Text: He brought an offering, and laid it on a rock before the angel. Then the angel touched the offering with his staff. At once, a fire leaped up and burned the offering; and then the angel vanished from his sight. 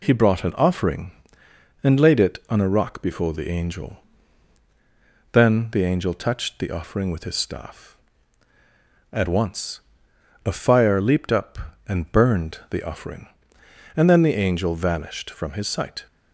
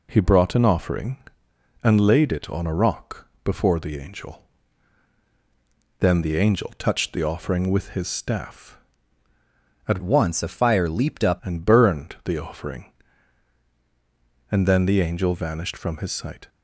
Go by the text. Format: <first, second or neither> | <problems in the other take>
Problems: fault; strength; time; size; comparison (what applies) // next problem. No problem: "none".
first | pauses between "rock" and "before"; slight; at 3.2 s; 0.16 s long // changes voice from "once" to "up"; from 10.0 to 11.3 s; 1.3 s long